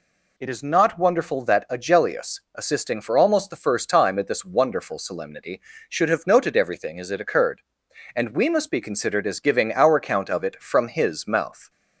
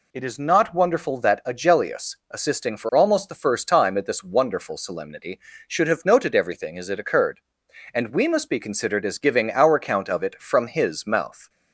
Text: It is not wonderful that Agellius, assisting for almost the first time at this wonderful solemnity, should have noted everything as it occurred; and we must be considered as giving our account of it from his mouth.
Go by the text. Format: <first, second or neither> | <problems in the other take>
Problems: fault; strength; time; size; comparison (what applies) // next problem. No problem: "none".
neither | none